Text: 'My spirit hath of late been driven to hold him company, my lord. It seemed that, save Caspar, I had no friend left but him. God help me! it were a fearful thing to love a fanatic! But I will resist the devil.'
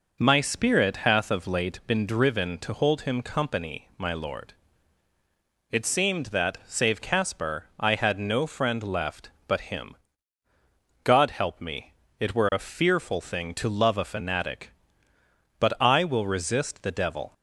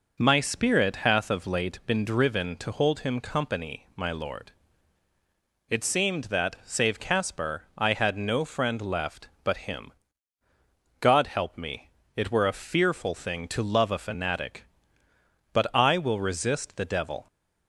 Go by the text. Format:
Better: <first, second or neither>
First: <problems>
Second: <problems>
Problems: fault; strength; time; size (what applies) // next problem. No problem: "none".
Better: neither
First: none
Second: none